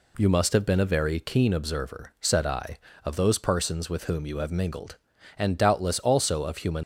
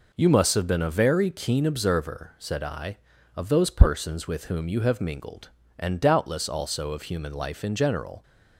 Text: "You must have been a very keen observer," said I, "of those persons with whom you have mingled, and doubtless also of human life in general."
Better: second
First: stops before "life in general"; at 6.8 s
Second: none

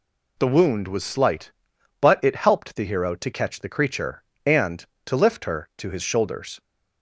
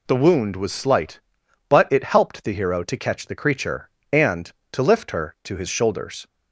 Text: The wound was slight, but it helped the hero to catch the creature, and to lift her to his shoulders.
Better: neither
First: none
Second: none

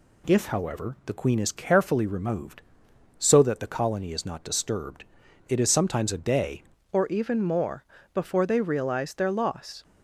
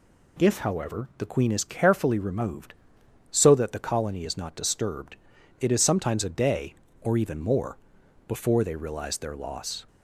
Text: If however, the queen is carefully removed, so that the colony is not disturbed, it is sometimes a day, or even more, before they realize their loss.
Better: second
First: changes voice at "or"; from 6.9 s on; 2.9 s long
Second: none

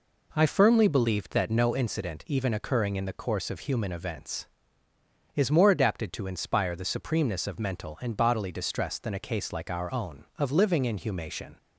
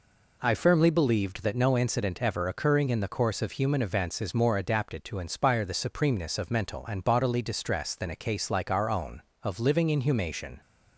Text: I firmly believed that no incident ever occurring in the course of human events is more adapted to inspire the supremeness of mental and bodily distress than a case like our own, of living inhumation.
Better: second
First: says "even" for "ever"; at 2.2 s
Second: none

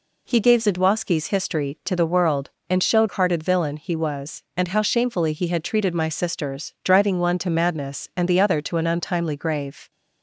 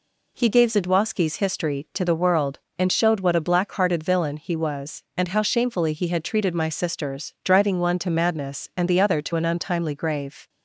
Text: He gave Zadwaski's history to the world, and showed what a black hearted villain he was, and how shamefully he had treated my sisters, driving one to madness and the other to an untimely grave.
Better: second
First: skips "what a black"; at 3.0 s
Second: none

